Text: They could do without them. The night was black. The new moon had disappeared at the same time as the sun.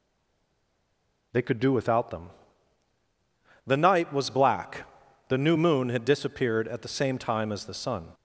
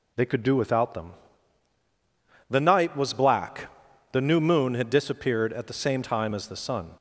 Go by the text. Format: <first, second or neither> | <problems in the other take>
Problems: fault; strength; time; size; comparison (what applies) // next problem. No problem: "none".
second | stays silent before the first word; noticeable; until 1.3 s; 1.3 s long